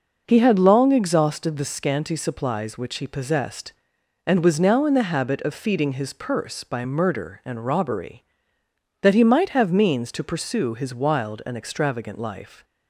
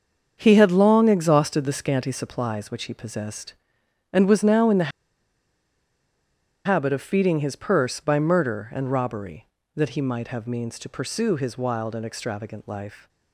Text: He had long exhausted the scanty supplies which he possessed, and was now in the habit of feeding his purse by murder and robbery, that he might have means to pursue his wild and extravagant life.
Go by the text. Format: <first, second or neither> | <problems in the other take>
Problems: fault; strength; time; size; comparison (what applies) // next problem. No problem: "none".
first | starts louder than the rest; strong; until 1.4 s; 7 dB // pauses between "the" and "habit"; strong; at 4.9 s; 1.7 s long